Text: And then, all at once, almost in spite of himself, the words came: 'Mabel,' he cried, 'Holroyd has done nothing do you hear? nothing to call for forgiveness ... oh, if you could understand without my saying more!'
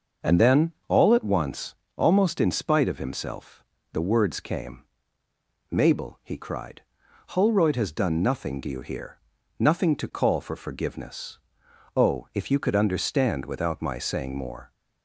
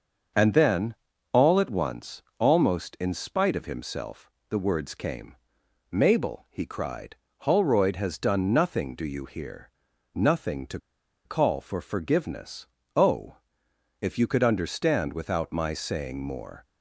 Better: first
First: none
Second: starts louder than the rest; until 1.7 s; 6.5 dB // pauses between "to" and "call"; noticeable; at 10.7 s; 0.47 s long

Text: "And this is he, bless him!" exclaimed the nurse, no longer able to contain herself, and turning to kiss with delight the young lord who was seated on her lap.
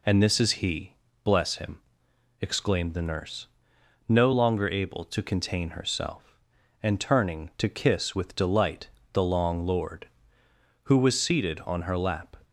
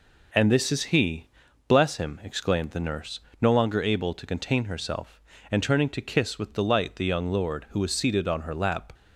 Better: second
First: pauses between "delight" and "the"; slight; at 8.8 s; 0.24 s long // says "long" for "young"; at 9.2 s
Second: none

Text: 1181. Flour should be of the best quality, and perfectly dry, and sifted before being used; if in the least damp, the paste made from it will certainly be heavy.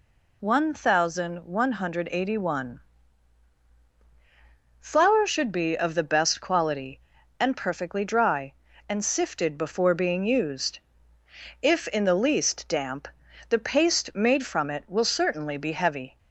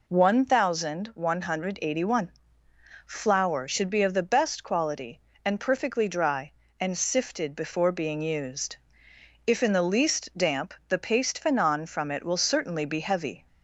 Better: first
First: none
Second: says "fanon" for "made"; at 11.4 s

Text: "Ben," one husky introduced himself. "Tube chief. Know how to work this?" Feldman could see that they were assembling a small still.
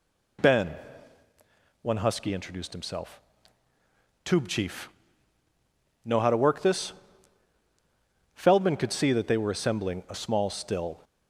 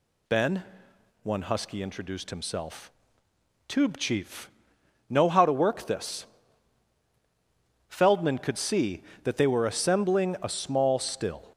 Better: neither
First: none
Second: none

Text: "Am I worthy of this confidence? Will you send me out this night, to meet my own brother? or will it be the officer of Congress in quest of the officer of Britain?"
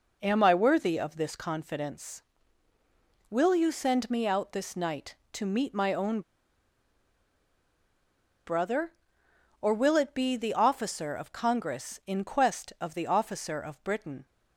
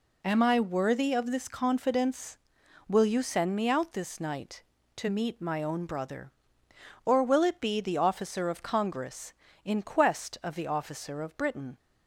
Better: second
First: pauses between "own" and "brother"; strong; at 6.2 s; 2.2 s long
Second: none

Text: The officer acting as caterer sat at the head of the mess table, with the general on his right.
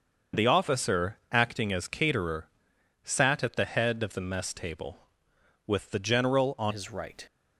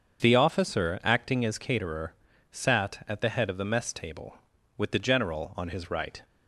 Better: second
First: starts louder than the rest; until 1.4 s; 6.5 dB // pauses between "caterer" and "sat"; noticeable; at 2.4 s; 0.56 s long // changes voice at "his"; from 6.7 s on; 0.5 s long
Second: starts louder than the rest; until 1.2 s; 7 dB // pauses between "caterer" and "sat"; at 2.1 s; 0.38 s long

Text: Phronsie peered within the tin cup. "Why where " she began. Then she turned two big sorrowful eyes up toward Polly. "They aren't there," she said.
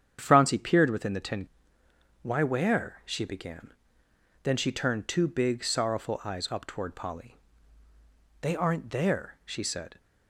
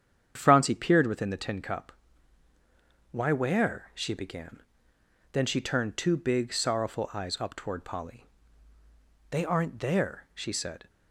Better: second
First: starts louder than the rest; strong; until 1.2 s; 8.5 dB // skips "cup"; at 1.8 s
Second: starts louder than the rest; strong; until 1.3 s; 8.5 dB

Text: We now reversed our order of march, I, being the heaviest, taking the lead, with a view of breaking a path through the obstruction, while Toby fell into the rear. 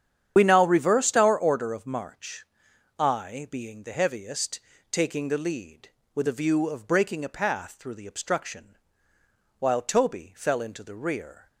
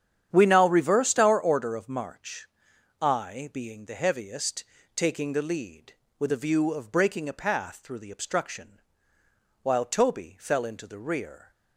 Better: second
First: loses the start of "We"; at 0.3 s; 60 ms // starts louder than the rest; strong; until 1.3 s; 9 dB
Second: starts louder than the rest; strong; until 1.3 s; 9 dB

